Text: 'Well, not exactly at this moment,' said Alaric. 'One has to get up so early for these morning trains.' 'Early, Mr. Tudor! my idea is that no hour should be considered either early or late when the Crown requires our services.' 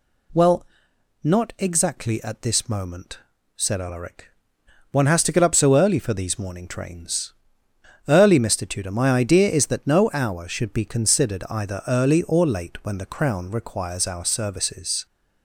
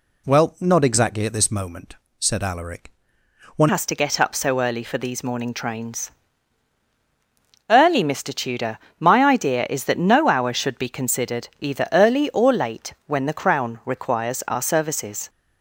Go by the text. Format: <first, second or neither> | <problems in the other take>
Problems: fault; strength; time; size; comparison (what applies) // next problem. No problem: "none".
first | changes voice at "has"; from 3.6 s on; 11.6 s long